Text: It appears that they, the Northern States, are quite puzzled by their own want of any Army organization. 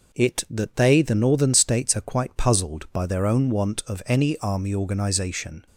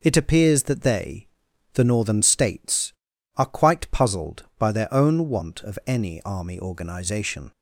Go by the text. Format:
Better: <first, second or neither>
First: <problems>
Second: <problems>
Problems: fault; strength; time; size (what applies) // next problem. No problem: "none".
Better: second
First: skips "appears"; at 0.4 s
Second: none